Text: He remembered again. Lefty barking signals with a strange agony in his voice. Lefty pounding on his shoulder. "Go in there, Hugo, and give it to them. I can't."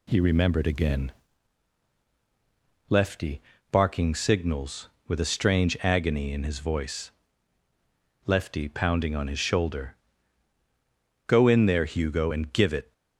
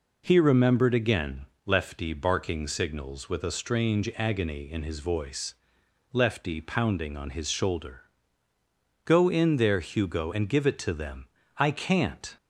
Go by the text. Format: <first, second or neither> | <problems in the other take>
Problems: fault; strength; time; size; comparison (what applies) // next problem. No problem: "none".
second | pauses between "Lefty" and "barking"; slight; at 3.4 s; 0.28 s long // stops before "to them I can't"; at 12.9 s